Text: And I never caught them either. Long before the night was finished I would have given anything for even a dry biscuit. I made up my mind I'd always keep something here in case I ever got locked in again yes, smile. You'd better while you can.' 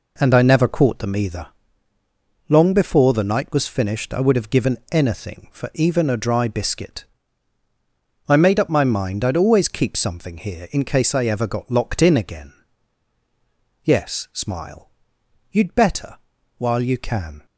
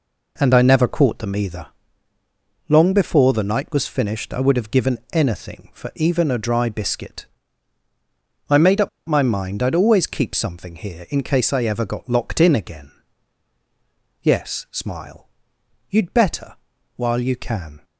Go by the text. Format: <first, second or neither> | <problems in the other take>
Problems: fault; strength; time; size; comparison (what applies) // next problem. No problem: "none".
first | pauses between "up" and "my"; slight; at 8.8 s; 0.18 s long // pauses between "again" and "yes"; strong; at 12.8 s; 1.3 s long; strong in the first // pauses between "better" and "while"; at 16.5 s; 0.42 s long; also in the first